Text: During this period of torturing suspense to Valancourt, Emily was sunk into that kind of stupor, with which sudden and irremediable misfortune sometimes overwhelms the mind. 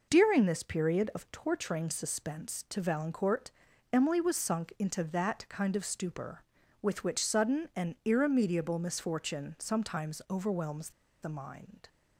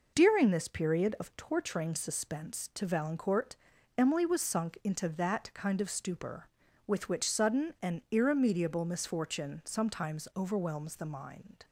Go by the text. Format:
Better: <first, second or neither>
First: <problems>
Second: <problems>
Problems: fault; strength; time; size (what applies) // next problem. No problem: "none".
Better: second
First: pauses between "overwhelms" and "the"; slight; at 10.9 s; 0.32 s long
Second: none